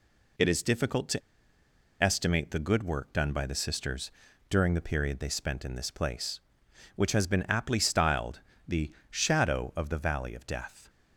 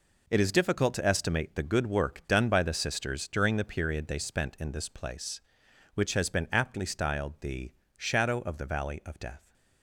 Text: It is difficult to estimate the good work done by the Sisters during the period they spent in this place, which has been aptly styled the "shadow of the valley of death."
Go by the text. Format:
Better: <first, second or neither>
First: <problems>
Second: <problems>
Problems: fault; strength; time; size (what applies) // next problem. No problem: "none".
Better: second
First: pauses between "to" and "estimate"; noticeable; at 1.2 s; 0.81 s long // pauses between "Sisters" and "during"; at 4.1 s; 0.38 s long // pauses between "styled" and "the"; slight; at 8.4 s; 0.26 s long // pauses between "the" and "shadow"; slight; at 8.9 s; 0.18 s long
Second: pauses between "the" and "shadow"; slight; at 7.7 s; 0.24 s long